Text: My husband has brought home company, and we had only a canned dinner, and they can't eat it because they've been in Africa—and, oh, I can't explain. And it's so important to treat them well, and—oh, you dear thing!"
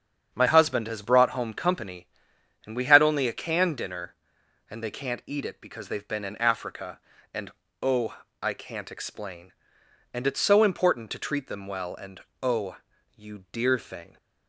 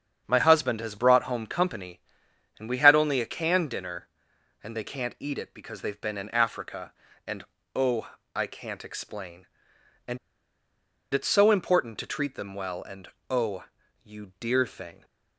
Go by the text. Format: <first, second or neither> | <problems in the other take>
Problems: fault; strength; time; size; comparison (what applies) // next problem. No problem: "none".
first | starts louder than the rest; strong; until 1.2 s; 7.5 dB; strong in the first // pauses between "And" and "it's"; noticeable; at 10.1 s; 0.96 s long